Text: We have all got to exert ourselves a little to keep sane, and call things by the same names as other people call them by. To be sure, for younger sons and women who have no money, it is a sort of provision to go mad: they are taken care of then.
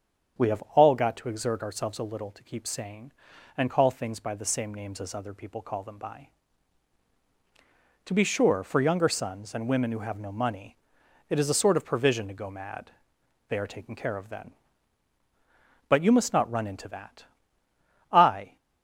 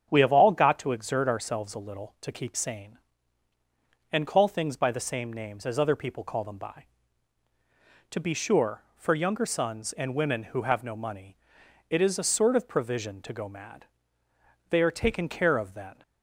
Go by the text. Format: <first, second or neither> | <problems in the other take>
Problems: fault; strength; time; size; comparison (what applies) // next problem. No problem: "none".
second | starts louder than the rest; strong; until 1.5 s; 7.5 dB; strong in the second // goes on to say "But you must not run into that I"; strong; from 15.8 s on; 2.6 s long